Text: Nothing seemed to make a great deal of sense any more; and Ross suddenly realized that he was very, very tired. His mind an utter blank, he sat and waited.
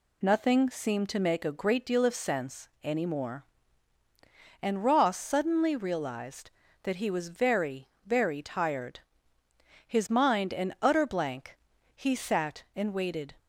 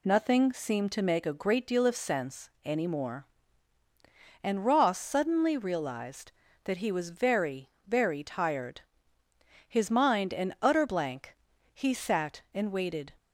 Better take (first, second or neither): neither